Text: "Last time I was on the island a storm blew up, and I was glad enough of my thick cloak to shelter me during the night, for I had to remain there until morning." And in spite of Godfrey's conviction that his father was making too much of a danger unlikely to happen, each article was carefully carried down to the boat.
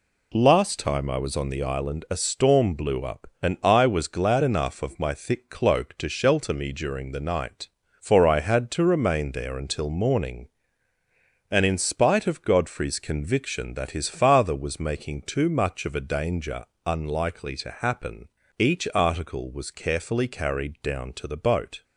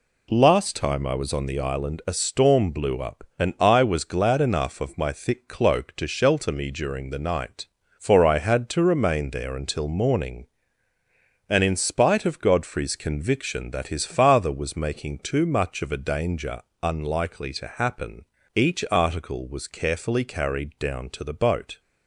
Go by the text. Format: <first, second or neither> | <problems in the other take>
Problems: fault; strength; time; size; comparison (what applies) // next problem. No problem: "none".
neither | pauses between "danger" and "unlikely"; slight; the same in both